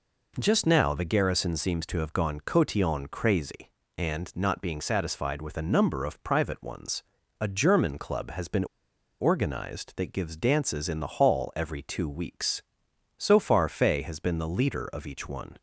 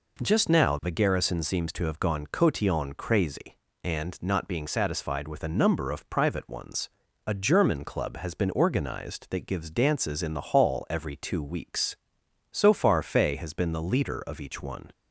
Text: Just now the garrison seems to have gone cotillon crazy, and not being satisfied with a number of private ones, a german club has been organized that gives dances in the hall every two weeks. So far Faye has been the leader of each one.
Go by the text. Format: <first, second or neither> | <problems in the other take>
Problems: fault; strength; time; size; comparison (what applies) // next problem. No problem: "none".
second | pauses between "been" and "organized"; noticeable; at 8.6 s; 0.55 s long